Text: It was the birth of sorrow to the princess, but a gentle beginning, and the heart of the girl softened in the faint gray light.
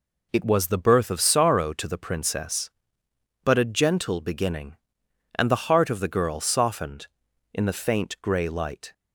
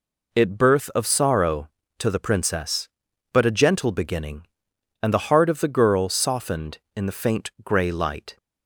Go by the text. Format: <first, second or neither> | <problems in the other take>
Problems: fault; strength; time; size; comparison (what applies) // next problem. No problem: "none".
first | skips "was the"; at 0.5 s